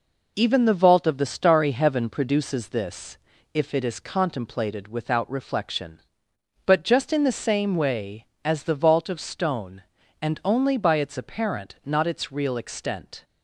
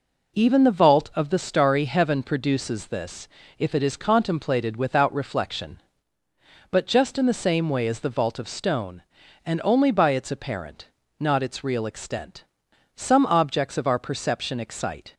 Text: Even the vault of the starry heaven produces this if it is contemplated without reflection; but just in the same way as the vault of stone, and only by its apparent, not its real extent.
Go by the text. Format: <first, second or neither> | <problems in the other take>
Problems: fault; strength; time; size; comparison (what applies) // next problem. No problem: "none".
first | pauses between "this" and "if"; slight; at 3.2 s; 0.32 s long; slight in the first // goes on to say "Some objects of our perception excite"; strong; from 12.9 s on; 2.1 s long